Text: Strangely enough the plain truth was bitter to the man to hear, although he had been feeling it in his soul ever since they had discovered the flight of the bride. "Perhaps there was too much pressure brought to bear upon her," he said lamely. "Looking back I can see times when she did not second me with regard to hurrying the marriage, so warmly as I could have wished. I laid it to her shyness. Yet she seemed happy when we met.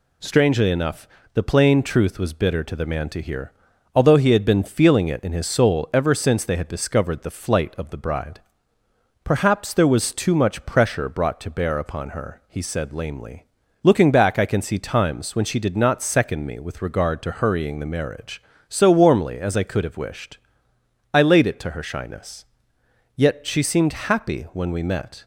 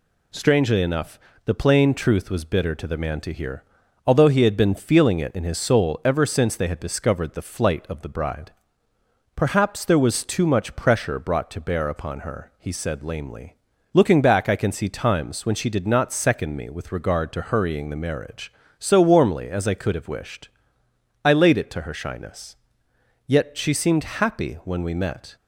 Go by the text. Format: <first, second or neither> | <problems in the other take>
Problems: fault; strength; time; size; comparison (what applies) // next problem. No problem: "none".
neither | pauses between "enough" and "the"; slight; the same in both